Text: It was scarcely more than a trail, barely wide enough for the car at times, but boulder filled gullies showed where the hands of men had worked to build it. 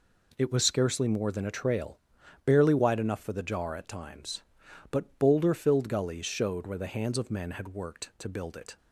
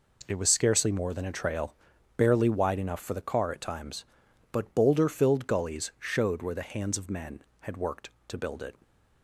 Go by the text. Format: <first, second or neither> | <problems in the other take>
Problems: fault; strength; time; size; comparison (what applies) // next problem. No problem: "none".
second | says "jar" for "car"; at 3.4 s